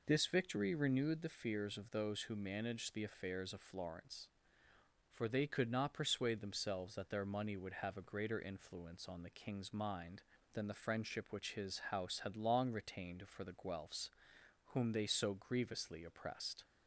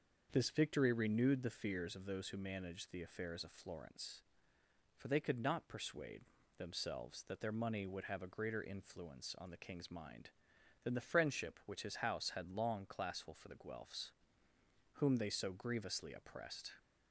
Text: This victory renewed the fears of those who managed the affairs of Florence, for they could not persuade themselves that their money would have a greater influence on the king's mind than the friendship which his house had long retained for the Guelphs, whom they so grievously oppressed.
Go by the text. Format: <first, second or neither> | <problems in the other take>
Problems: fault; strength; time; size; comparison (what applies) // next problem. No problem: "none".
first | starts louder than the rest; until 1.3 s; 6.5 dB // pauses between "persuade" and "themselves"; slight; at 6.2 s; 0.36 s long // says "classful" for "retained"; at 12.8 s